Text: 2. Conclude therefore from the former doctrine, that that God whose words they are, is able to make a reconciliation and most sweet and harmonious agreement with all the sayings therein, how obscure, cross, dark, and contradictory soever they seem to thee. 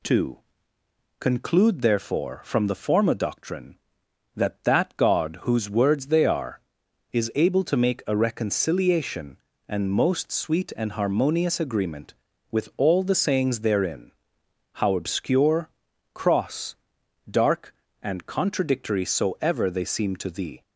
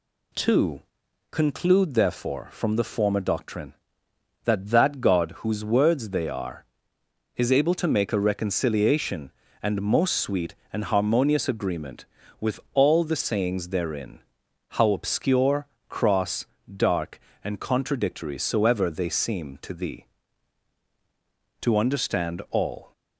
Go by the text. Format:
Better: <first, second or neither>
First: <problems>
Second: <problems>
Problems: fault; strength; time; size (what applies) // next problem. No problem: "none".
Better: first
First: none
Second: goes on to say "To understand all"; noticeable; from 21.6 s on; 1.3 s long